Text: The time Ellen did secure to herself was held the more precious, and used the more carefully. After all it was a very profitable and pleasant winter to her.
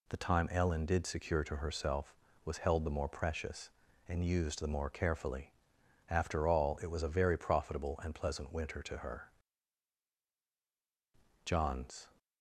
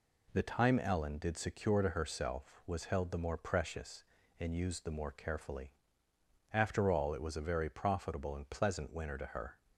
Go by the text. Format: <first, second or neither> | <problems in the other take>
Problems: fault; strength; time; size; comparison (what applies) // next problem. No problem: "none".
second | goes on to say "John's"; noticeable; from 11.4 s on; 0.62 s long